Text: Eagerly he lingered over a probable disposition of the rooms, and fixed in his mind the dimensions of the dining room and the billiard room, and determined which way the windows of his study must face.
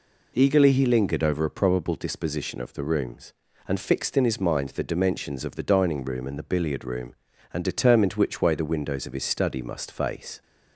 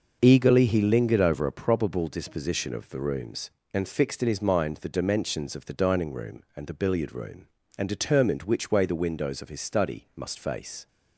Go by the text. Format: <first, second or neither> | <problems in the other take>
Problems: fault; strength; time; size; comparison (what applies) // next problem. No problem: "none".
neither | none